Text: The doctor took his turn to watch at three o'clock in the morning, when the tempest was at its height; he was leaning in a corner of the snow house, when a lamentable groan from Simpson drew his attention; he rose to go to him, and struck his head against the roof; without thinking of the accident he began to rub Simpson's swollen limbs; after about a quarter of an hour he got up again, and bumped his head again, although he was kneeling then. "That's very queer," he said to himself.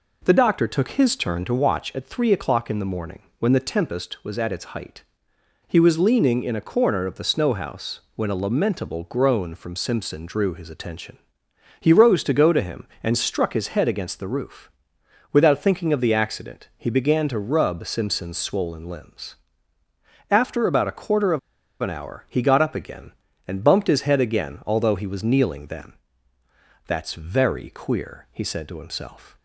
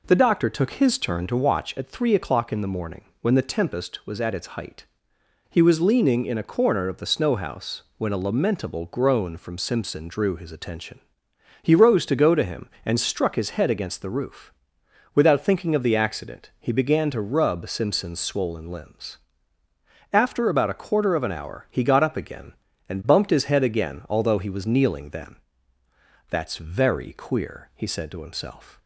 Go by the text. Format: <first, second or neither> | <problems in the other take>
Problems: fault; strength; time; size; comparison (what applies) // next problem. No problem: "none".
second | pauses between "of" and "an"; at 21.3 s; 0.42 s long